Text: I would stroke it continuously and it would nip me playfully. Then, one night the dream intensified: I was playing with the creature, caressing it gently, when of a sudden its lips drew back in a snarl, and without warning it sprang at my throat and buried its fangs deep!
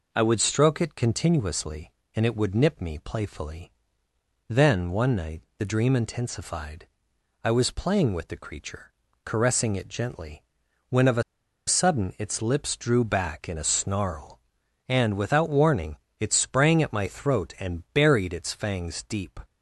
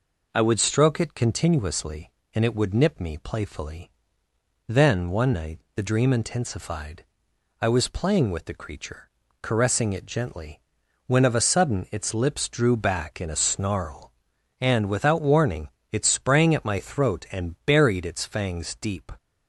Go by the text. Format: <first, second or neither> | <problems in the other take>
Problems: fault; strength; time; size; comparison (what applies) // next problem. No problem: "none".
second | pauses between "night" and "the"; slight; at 5.4 s; 0.16 s long; slight in the second // pauses between "a" and "sudden"; at 11.2 s; 0.44 s long // pauses between "warning" and "it"; slight; at 15.9 s; 0.24 s long; slight in the second